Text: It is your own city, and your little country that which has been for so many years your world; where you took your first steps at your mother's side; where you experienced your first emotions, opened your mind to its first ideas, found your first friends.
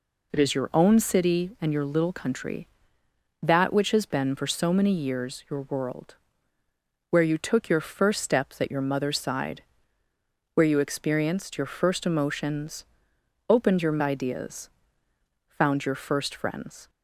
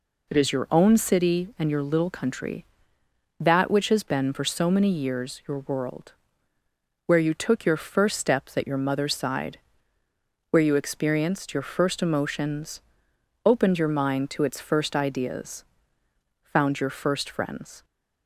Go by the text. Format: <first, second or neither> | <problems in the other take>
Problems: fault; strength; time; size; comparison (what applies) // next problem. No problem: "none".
second | skips "mind to its first"; at 13.9 s